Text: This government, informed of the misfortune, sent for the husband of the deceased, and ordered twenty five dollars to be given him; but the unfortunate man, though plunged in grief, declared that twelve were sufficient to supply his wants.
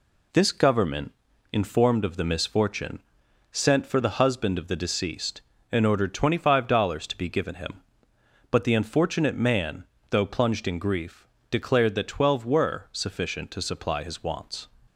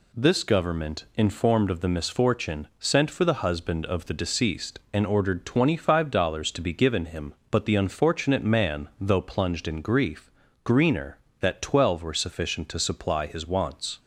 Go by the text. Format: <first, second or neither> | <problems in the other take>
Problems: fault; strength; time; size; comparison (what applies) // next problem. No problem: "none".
first | says "greener" for "declared"; at 10.6 s